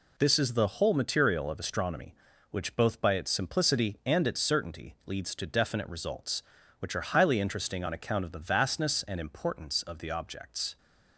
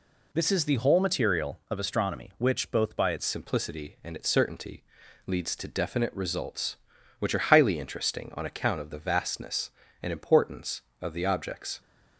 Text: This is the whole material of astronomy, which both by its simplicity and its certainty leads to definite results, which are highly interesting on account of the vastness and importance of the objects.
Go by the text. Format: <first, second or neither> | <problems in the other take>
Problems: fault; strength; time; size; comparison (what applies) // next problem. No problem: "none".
first | changes voice at "simplicity"; from 3.2 s on; 8.6 s long // pauses between "certainty" and "leads"; at 4.8 s; 0.42 s long